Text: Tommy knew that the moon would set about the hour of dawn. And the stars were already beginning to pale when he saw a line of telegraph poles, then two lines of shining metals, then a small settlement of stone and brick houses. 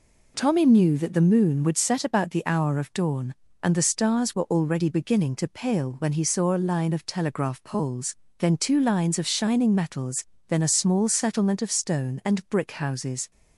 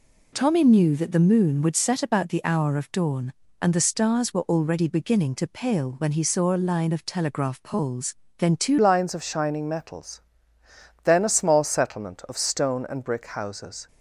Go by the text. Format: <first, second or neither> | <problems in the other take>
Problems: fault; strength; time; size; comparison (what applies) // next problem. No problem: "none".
first | changes voice at "lines"; from 8.7 s on; 5.1 s long